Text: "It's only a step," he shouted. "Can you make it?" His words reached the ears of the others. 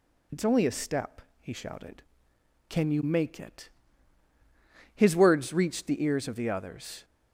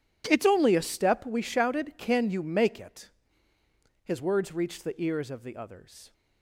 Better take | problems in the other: first | says "we" for "he"; at 1.2 s

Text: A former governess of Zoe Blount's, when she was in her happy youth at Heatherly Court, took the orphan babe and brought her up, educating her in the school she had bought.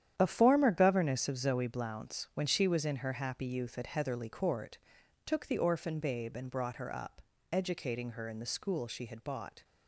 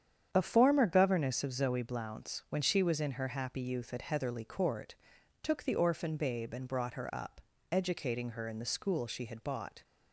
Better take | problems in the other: second | gets quieter; strong; throughout; 10.5 dB // starts louder than the rest; strong; until 1.1 s; 10 dB; strong in the second

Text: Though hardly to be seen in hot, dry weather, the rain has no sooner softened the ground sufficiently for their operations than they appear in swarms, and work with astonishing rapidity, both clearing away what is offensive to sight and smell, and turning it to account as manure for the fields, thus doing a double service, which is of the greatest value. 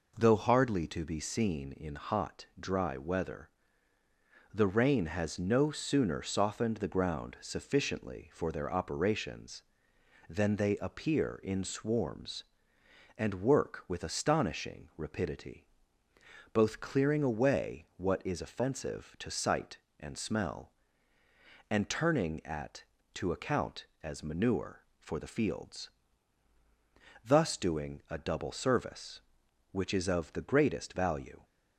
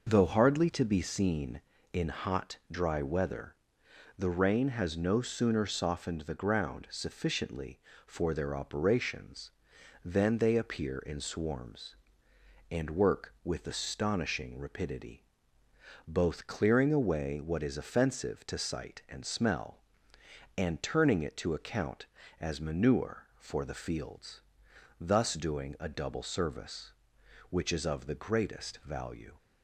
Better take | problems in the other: second | says "at" for "it"; at 22.4 s

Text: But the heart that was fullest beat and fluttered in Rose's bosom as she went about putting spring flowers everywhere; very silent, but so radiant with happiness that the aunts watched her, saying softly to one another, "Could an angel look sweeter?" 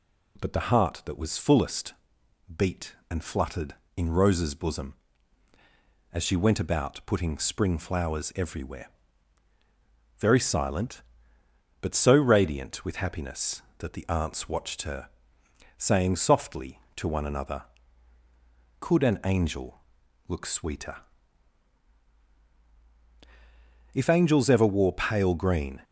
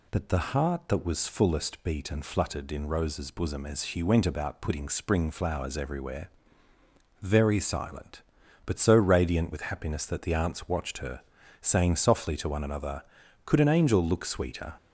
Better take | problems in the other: second | pauses between "fullest" and "beat"; noticeable; at 1.9 s; 0.60 s long // pauses between "angel" and "look"; noticeable; at 19.8 s; 0.48 s long // goes on to say "If angels ever wore pale green"; strong; from 23.9 s on; 1.8 s long

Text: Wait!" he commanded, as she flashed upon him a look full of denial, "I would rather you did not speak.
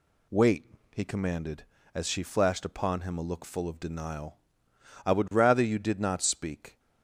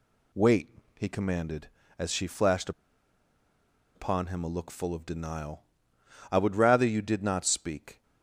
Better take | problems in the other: first | pauses between "flashed" and "upon"; strong; at 2.7 s; 1.2 s long

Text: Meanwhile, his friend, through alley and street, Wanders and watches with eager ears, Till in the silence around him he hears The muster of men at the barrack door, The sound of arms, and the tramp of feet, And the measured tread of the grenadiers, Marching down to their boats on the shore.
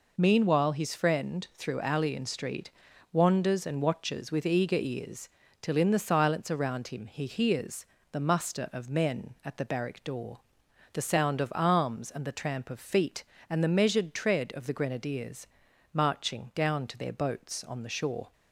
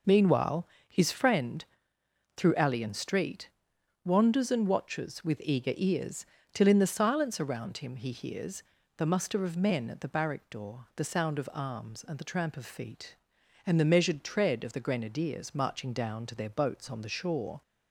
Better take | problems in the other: neither | pauses between "hears" and "The"; slight; the same in both

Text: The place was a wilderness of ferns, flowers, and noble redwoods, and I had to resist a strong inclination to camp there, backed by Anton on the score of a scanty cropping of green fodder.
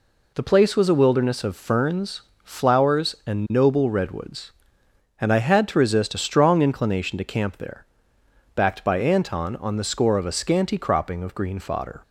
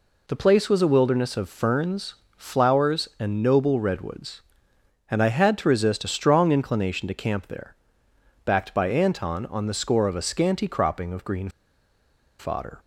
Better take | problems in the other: first | pauses between "green" and "fodder"; noticeable; at 11.4 s; 0.90 s long

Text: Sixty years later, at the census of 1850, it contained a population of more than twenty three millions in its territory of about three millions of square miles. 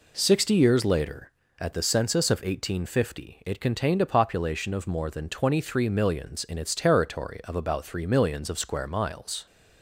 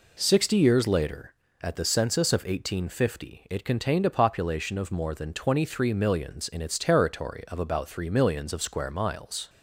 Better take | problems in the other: neither | none

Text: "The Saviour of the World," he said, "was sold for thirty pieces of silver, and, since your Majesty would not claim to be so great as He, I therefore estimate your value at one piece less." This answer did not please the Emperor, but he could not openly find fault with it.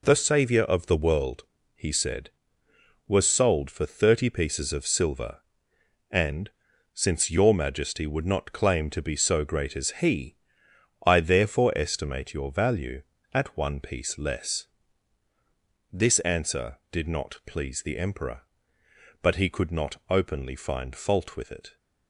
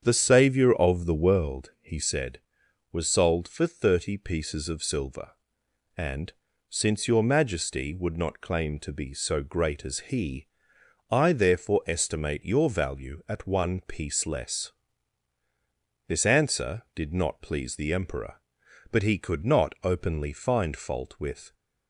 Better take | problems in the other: first | starts louder than the rest; strong; until 1.0 s; 8 dB // stops before "it"; at 21.5 s

